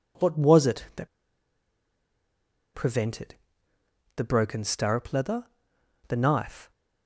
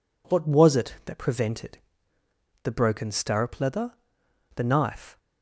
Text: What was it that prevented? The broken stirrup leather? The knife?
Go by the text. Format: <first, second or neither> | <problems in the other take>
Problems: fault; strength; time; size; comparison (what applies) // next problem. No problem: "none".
second | pauses between "that" and "prevented"; strong; at 1.0 s; 1.6 s long